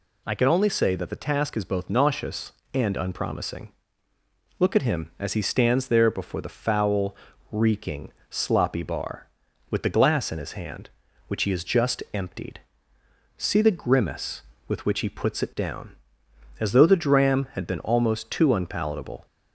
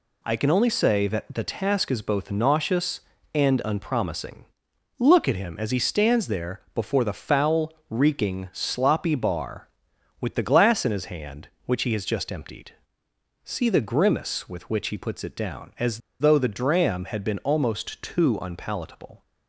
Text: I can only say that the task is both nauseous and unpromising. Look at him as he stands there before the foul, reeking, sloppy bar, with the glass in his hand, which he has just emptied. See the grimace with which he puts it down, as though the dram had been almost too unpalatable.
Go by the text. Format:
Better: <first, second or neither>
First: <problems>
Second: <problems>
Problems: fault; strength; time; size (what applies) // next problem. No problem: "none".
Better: first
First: none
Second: pauses between "there" and "before"; slight; at 6.5 s; 0.16 s long // pauses between "as" and "though"; slight; at 16.0 s; 0.21 s long